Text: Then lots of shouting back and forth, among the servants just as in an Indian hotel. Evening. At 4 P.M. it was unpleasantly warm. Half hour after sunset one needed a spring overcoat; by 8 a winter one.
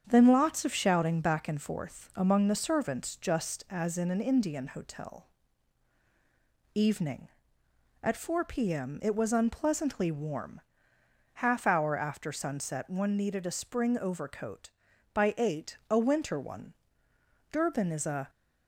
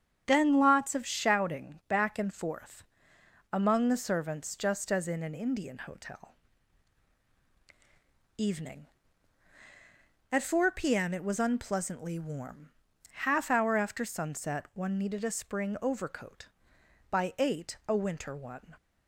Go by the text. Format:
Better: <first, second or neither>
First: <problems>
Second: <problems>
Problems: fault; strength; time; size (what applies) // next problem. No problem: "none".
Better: second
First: starts louder than the rest; strong; until 1.0 s; 8 dB // goes on to say "Durban is a"; noticeable; from 17.5 s on; 0.78 s long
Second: starts louder than the rest; strong; until 1.2 s; 8.5 dB